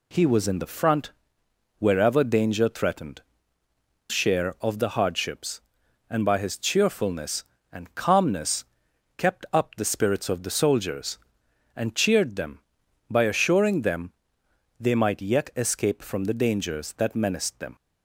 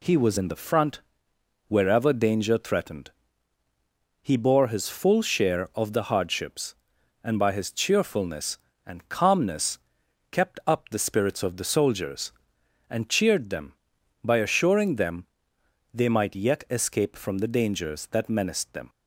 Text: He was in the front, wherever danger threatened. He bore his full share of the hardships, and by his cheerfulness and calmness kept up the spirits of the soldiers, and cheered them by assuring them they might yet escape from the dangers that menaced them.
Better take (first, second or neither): second